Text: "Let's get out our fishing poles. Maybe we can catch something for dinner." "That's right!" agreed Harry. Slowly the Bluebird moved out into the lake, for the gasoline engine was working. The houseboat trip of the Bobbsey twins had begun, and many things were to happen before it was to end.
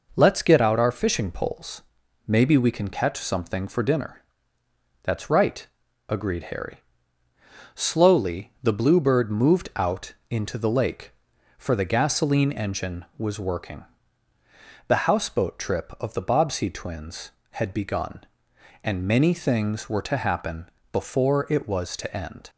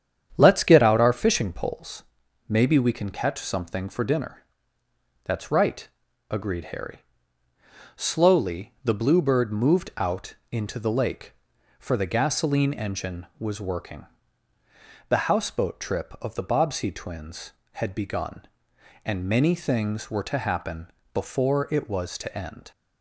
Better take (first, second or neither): first